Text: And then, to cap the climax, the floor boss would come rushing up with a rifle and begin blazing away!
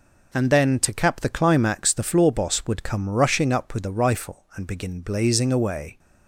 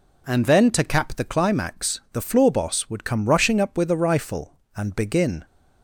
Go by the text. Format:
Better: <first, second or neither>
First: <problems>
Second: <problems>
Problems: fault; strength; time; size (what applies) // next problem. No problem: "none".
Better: first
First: none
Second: stops before "blazing away"; at 5.4 s